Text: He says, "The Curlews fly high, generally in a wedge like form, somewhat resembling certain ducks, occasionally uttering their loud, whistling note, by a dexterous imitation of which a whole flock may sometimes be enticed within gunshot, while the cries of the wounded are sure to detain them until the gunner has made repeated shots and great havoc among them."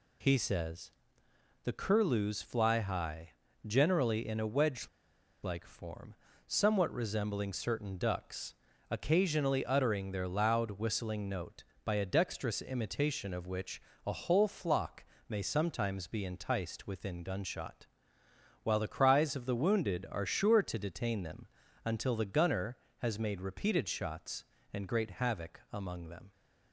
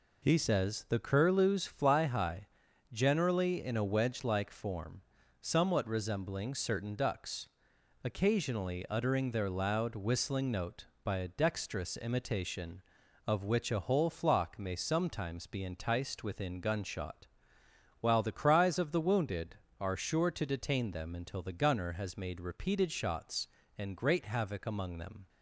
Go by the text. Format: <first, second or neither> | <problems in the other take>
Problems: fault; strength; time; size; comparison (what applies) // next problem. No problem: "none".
second | pauses between "wedge" and "like"; noticeable; at 4.8 s; 0.57 s long // pauses between "which" and "a"; slight; at 13.7 s; 0.26 s long // pauses between "flock" and "may"; slight; at 15.0 s; 0.24 s long // pauses between "them" and "until"; at 21.4 s; 0.38 s long